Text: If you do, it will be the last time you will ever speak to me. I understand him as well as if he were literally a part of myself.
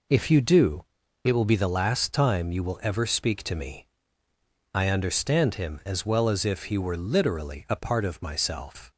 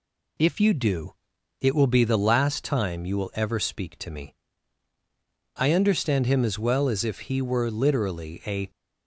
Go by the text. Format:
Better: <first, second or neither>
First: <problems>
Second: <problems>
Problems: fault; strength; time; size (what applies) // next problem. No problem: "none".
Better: first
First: none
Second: stops before "part of myself"; at 8.6 s